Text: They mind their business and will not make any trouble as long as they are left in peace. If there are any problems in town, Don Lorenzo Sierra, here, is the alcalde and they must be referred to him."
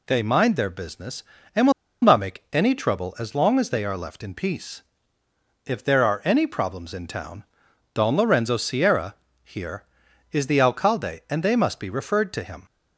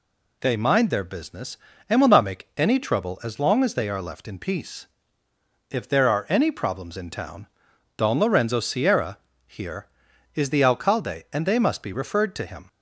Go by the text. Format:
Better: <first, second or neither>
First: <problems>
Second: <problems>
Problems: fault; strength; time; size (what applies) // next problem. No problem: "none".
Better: second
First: pauses between "will" and "not"; slight; at 1.7 s; 0.30 s long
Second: none